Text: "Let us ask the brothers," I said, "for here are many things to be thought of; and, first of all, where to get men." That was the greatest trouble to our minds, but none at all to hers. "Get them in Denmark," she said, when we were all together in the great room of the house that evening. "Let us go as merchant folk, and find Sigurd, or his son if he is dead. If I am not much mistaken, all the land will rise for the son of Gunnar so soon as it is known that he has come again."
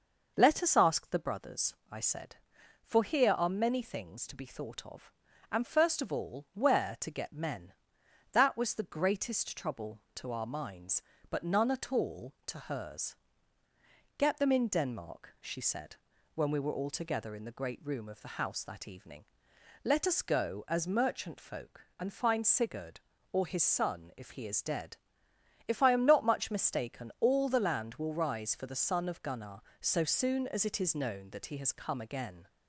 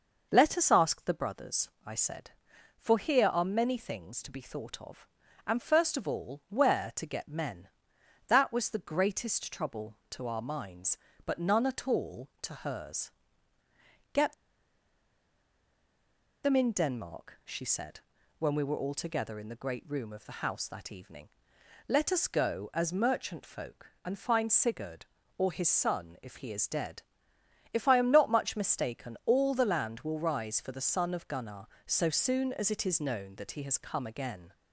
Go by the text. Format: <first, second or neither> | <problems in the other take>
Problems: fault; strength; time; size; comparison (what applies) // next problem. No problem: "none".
first | pauses between "Get" and "them"; strong; at 14.3 s; 2.1 s long